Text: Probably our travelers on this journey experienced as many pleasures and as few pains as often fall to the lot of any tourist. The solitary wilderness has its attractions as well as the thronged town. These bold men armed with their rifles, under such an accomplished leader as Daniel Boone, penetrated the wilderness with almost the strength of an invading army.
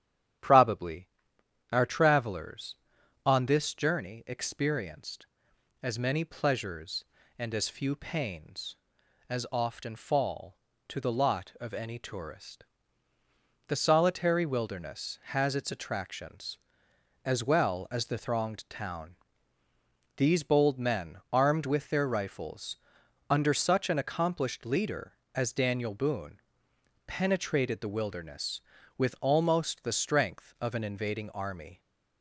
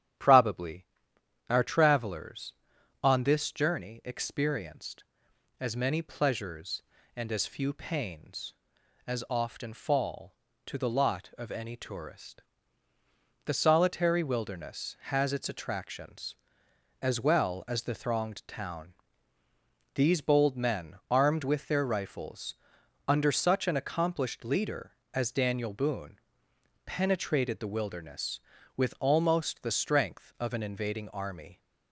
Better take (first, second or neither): neither